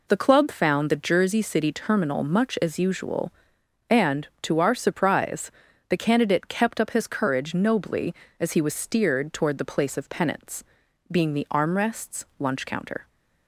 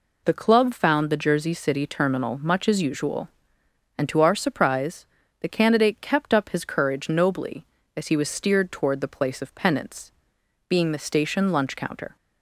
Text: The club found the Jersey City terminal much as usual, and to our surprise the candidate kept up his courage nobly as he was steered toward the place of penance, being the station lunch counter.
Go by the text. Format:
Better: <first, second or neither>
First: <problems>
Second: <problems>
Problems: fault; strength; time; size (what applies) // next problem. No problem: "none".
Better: second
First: pauses between "surprise" and "the"; at 5.4 s; 0.40 s long // says "armrests" for "station"; at 11.4 s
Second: pauses between "surprise" and "the"; slight; at 5.0 s; 0.36 s long